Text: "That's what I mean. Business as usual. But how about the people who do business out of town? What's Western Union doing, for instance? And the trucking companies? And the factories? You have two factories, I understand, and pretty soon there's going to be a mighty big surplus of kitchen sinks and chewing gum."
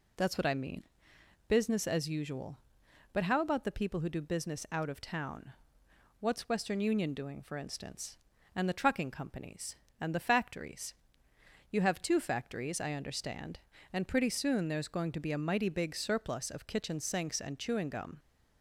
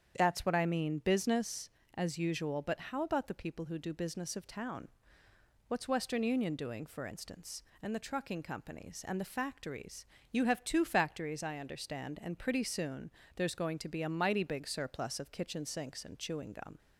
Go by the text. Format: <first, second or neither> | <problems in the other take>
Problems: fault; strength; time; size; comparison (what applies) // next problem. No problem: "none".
first | starts louder than the rest; strong; until 1.1 s; 8 dB // skips "out"; at 4.3 s // pauses between "soon" and "there's"; slight; at 13.0 s; 0.24 s long